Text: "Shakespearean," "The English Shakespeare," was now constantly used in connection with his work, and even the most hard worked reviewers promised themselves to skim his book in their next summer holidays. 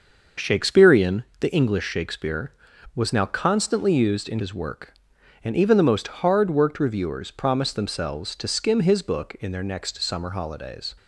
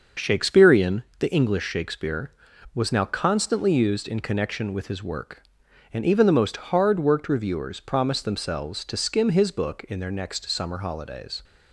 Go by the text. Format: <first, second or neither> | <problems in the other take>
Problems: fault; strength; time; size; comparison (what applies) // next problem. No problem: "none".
second | starts louder than the rest; noticeable; until 1.5 s; 6 dB; also in the second // skips "connection with"; at 4.3 s